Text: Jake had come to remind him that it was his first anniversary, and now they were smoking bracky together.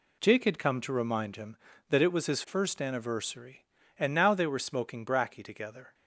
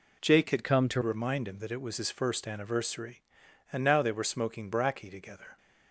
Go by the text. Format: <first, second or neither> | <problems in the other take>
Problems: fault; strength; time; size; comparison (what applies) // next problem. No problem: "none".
first | changes voice from "come" to "to"; from 0.6 to 1.0 s; 0.4 s long